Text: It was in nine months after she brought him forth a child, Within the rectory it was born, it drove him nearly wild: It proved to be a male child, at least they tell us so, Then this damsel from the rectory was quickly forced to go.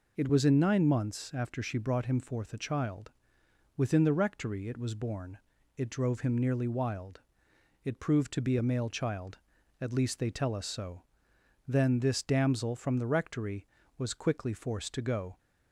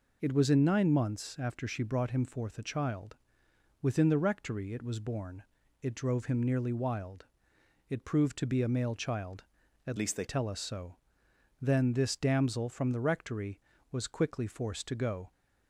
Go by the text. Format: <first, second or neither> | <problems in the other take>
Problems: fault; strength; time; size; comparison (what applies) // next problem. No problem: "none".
first | changes voice from "least" to "they"; from 9.9 to 10.2 s; 0.3 s long